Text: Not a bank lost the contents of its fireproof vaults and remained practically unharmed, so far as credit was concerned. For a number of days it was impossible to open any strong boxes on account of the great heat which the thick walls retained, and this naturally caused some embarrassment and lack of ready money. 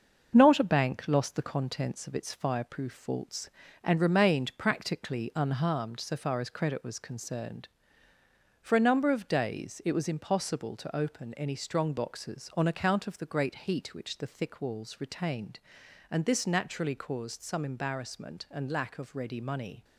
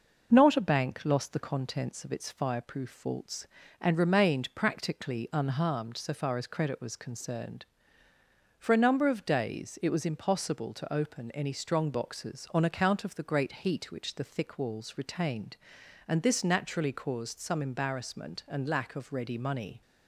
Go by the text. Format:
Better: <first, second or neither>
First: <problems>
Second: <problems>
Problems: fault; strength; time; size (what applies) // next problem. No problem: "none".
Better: second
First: gets quieter; noticeable; throughout; 5 dB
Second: none